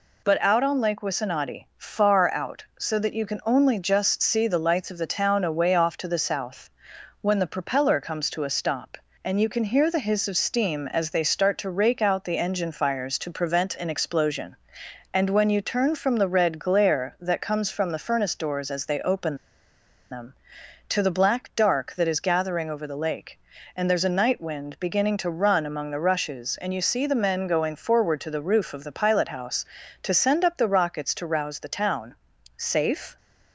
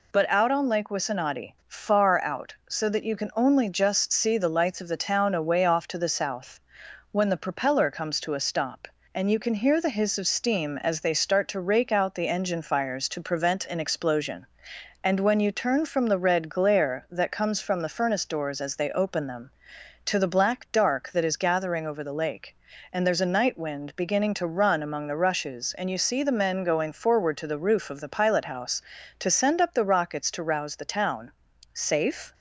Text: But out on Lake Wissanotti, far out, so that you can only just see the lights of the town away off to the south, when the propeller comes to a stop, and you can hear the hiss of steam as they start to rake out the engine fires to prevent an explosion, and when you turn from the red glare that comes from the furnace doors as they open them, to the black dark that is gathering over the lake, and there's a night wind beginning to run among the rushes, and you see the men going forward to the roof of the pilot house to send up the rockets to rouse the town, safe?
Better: second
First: pauses between "open" and "them"; noticeable; at 19.3 s; 0.76 s long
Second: none

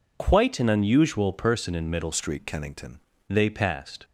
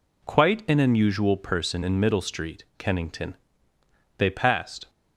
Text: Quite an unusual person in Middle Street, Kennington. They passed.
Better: second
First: changes voice from "Street" to "Kennington"; from 2.1 to 2.9 s; 0.8 s long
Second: none

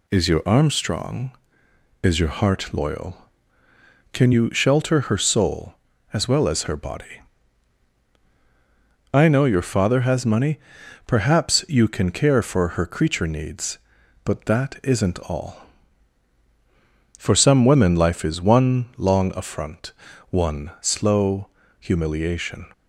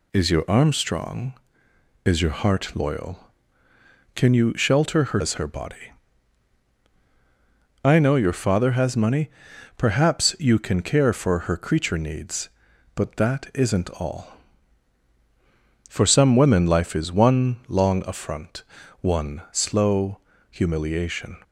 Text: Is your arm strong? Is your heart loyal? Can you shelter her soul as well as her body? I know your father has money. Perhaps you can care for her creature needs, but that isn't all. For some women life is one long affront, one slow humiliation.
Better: first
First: pauses between "slow" and "humiliation"; slight; at 21.4 s; 0.32 s long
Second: skips "soul as well"; at 5.2 s // pauses between "slow" and "humiliation"; slight; at 20.1 s; 0.32 s long

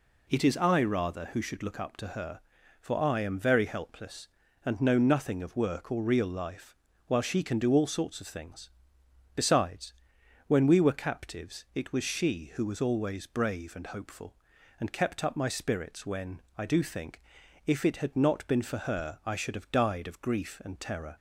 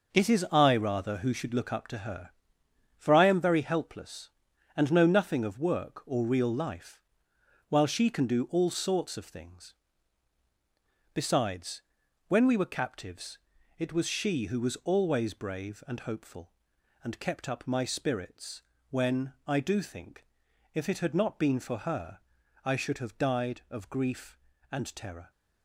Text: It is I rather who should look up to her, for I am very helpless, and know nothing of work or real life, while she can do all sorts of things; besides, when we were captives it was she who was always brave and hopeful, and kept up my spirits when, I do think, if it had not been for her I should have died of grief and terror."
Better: first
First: none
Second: gets quieter; strong; throughout; 8 dB // pauses between "captives" and "it"; at 13.3 s; 0.40 s long // pauses between "spirits" and "when"; slight; at 18.6 s; 0.28 s long // pauses between "her" and "I"; noticeable; at 22.1 s; 0.46 s long

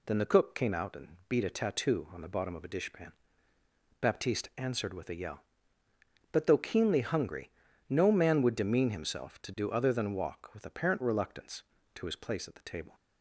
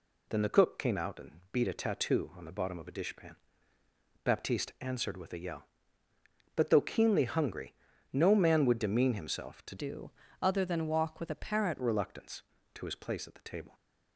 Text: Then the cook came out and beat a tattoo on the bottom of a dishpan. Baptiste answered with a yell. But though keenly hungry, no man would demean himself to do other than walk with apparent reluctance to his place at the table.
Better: first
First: none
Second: changes voice from "do" to "apparent"; from 9.7 to 11.7 s; 2.0 s long // pauses between "do" and "other"; slight; at 10.1 s; 0.30 s long

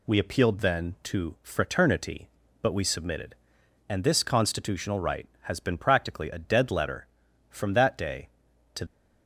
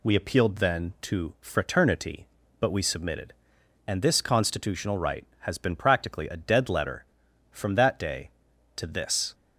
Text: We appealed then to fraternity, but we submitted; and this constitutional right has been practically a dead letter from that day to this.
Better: second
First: stops before "this"; at 8.8 s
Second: none

